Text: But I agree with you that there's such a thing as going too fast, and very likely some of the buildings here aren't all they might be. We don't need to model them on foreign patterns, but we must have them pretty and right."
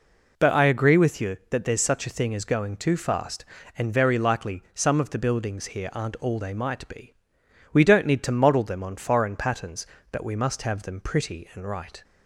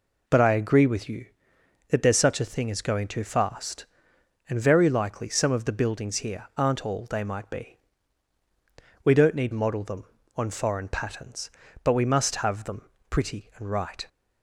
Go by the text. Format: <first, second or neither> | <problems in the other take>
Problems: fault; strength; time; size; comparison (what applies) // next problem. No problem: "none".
first | skips "to"; at 9.5 s // pauses between "them" and "pretty"; slight; at 12.8 s; 0.28 s long